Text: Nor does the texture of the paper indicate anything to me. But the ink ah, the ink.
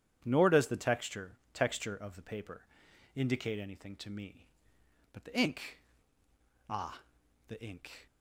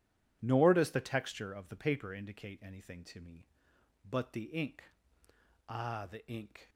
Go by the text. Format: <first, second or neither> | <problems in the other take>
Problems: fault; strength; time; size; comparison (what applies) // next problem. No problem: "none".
second | starts louder than the rest; strong; until 1.2 s; 9.5 dB // says "texture" twice; at 1.5 s // pauses between "paper" and "indicate"; noticeable; at 2.6 s; 0.54 s long // pauses between "ink" and "ah"; noticeable; at 5.7 s; 0.90 s long; noticeable in the second